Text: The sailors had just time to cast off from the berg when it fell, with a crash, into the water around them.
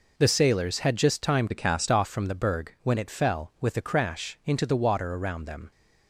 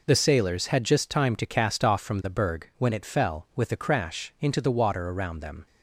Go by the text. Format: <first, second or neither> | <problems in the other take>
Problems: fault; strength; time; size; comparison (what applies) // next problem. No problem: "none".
second | changes voice from "to" to "cast"; from 1.5 to 1.8 s; 0.3 s long